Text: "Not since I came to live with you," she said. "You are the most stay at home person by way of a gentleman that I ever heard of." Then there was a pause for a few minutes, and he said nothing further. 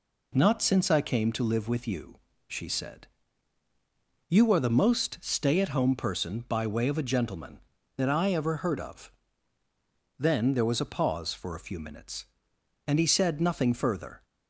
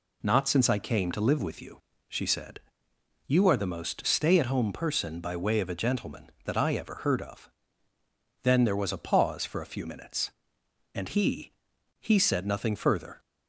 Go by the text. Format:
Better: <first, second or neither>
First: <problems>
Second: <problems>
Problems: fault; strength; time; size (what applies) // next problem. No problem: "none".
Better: first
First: none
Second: says "he" twice; at 12.0 s